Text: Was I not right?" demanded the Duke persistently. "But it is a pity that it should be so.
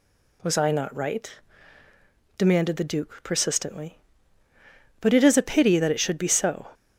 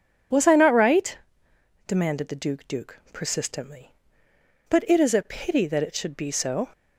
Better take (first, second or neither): first